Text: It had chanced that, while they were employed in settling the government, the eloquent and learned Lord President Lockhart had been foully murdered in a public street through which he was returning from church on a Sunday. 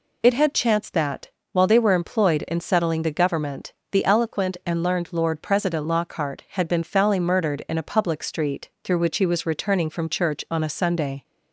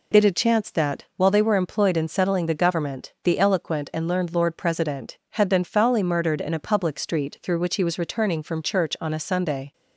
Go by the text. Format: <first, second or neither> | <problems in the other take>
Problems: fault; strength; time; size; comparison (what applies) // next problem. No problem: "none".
first | skips "Lockhart"; at 5.2 s